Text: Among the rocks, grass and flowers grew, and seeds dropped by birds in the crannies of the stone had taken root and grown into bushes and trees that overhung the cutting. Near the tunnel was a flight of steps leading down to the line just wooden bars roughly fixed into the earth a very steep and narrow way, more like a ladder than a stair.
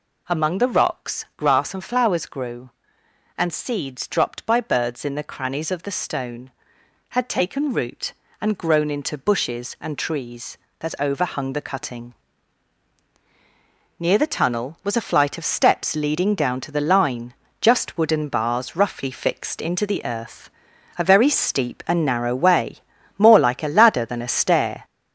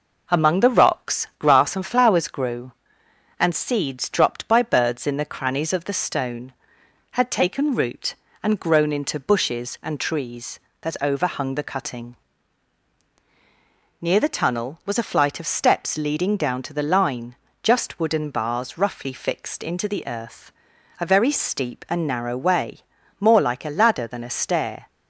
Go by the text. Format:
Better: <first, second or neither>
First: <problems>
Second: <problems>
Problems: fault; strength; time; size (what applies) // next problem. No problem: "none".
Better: second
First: gets louder; noticeable; throughout; 6 dB // pauses between "line" and "just"; slight; at 17.3 s; 0.28 s long // pauses between "earth" and "a"; noticeable; at 20.4 s; 0.50 s long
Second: pauses between "line" and "just"; slight; at 17.3 s; 0.28 s long // pauses between "earth" and "a"; noticeable; at 20.5 s; 0.50 s long